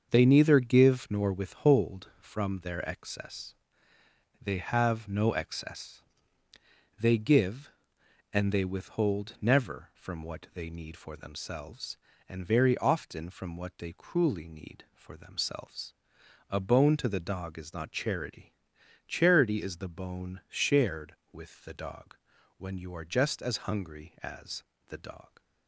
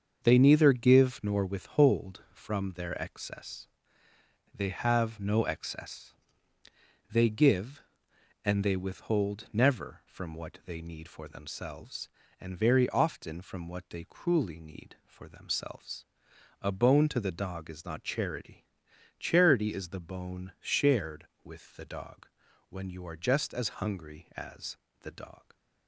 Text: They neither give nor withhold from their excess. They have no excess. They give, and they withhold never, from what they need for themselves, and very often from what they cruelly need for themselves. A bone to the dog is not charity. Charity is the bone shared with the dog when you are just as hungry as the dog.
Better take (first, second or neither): neither